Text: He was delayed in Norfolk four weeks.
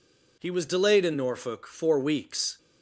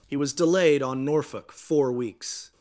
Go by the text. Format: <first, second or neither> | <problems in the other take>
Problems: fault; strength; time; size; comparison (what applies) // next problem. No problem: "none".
first | says "on" for "in"; at 0.8 s